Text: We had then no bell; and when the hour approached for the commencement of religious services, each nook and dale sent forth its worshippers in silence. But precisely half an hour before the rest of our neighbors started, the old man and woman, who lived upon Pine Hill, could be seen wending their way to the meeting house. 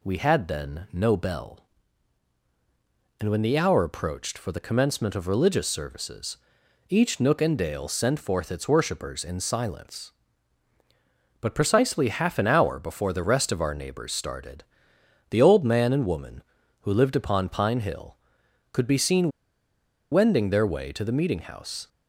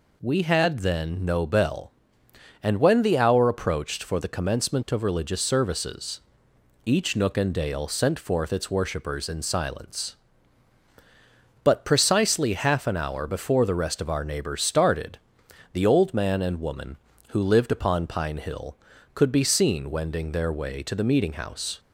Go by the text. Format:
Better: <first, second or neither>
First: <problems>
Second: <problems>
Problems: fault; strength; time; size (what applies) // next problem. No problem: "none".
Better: second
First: pauses between "seen" and "wending"; noticeable; at 19.3 s; 0.81 s long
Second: none